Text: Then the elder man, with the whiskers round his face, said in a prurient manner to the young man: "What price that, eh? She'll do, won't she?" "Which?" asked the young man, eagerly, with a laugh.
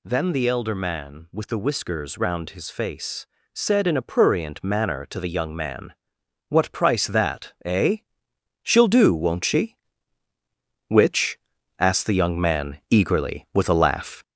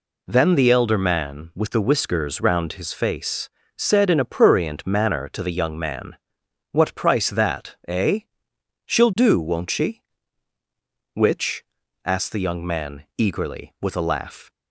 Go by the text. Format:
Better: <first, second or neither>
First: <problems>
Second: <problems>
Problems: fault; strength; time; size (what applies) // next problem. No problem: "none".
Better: second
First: gets louder; throughout; 4 dB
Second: none